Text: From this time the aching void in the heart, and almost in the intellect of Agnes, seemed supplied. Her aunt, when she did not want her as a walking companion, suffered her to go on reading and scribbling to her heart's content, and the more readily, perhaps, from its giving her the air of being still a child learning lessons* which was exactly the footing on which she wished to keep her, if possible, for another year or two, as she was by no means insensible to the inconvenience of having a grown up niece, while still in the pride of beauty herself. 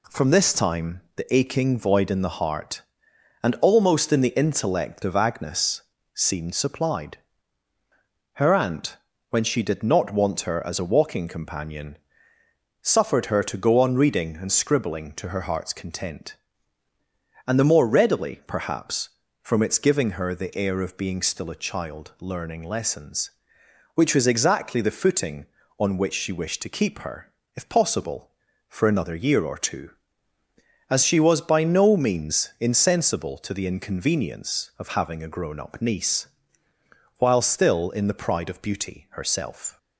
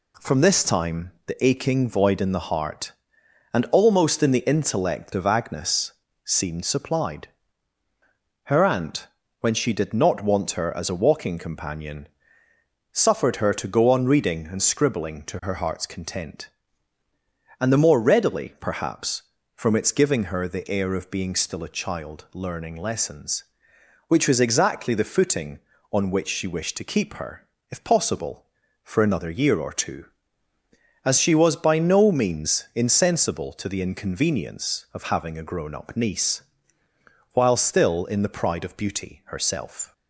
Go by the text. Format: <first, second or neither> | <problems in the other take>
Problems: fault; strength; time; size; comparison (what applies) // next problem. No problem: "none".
neither | pauses between "time" and "the"; slight; the same in both